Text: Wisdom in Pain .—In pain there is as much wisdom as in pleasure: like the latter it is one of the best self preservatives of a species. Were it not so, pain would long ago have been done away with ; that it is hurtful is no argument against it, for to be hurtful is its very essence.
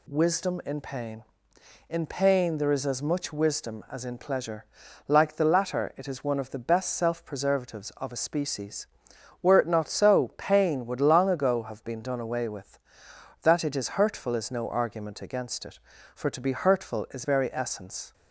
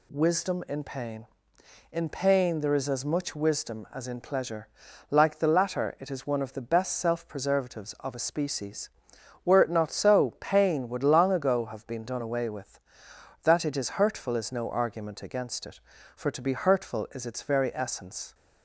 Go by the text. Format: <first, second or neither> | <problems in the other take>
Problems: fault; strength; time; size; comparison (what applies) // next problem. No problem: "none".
second | skips "its"; at 17.2 s